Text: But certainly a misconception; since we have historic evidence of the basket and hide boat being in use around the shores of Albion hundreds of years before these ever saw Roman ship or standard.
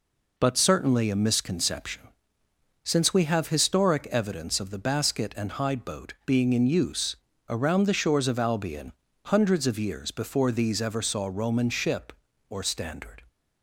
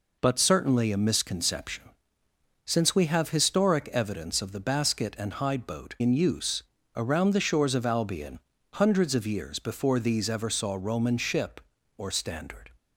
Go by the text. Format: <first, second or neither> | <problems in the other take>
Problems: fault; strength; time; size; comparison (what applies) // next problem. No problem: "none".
first | skips "being"; at 5.9 s // pauses between "use" and "around"; slight; at 6.6 s; 0.34 s long; slight in the first // pauses between "Albion" and "hundreds"; slight; at 8.3 s; 0.36 s long; slight in the first